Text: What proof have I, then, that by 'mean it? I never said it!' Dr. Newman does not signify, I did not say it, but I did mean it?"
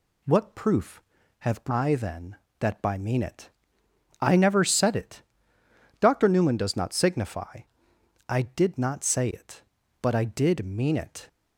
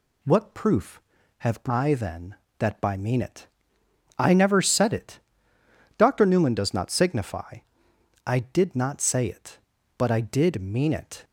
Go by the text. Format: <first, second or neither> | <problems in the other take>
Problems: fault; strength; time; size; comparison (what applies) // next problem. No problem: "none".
neither | none